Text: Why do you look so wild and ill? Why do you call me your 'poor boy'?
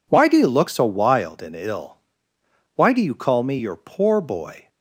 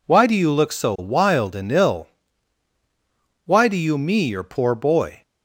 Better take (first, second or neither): first